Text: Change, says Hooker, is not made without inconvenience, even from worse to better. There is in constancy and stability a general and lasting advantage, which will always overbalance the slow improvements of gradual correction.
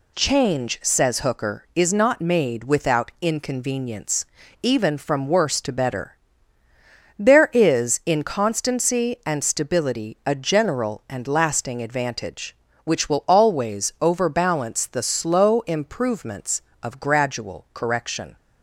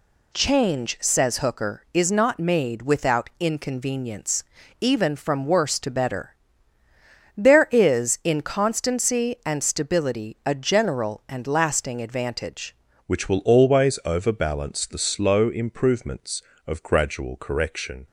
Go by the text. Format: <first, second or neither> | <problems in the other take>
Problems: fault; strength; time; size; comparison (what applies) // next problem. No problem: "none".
first | changes voice at "which"; from 13.0 s on; 5.0 s long